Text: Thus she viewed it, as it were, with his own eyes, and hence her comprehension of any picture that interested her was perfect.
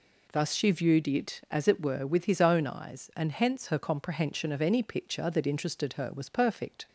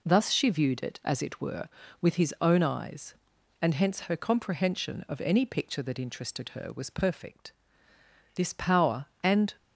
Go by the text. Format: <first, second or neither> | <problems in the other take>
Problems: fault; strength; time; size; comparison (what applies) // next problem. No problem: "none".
first | goes on to say "This power and"; noticeable; from 8.3 s on; 1.1 s long